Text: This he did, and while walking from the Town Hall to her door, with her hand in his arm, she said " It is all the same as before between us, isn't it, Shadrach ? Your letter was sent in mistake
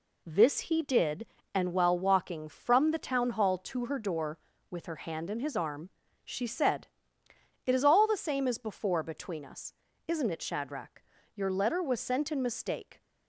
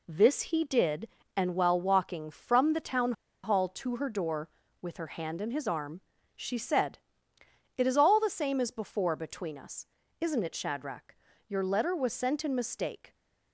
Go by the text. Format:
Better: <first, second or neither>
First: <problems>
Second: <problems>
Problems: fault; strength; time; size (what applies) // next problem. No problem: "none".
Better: first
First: none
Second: pauses between "Town" and "Hall"; slight; at 3.1 s; 0.30 s long